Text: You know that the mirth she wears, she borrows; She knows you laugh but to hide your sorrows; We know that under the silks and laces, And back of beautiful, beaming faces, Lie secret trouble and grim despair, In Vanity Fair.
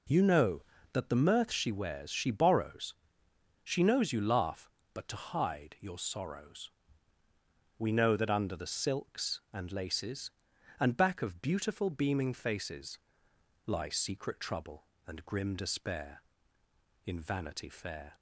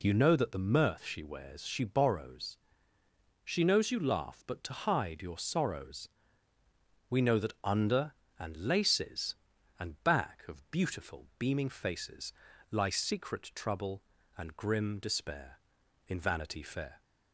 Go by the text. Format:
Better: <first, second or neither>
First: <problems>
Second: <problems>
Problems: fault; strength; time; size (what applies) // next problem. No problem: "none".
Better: first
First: none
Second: skips "the silks"; at 8.2 s